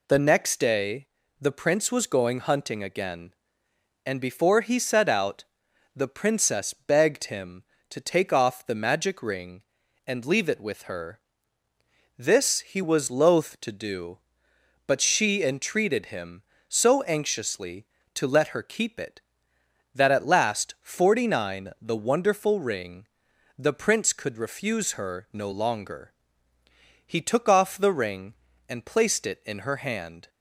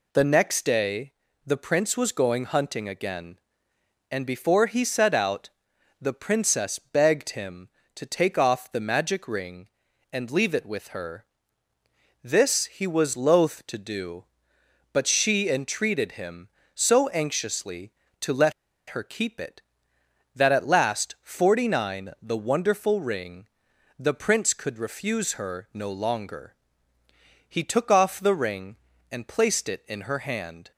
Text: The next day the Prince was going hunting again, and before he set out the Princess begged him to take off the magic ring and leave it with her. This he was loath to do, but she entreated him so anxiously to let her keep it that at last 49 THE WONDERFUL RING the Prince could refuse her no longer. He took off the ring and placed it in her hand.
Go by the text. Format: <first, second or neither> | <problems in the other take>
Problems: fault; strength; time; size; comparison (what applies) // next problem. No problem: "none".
first | pauses between "day" and "the"; slight; at 1.1 s; 0.34 s long; slight in the first // pauses between "out" and "the"; noticeable; at 5.5 s; 0.50 s long; noticeable in the first // pauses between "let" and "her"; at 18.5 s; 0.36 s long // pauses between "RING" and "the"; noticeable; at 23.4 s; 0.50 s long; noticeable in the first